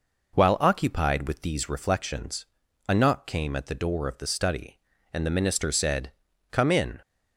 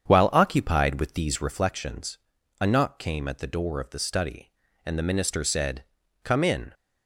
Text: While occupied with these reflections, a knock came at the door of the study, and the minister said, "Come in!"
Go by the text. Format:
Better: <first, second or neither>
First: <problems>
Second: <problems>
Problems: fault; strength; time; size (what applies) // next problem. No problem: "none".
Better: first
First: none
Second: starts louder than the rest; strong; until 1.6 s; 8 dB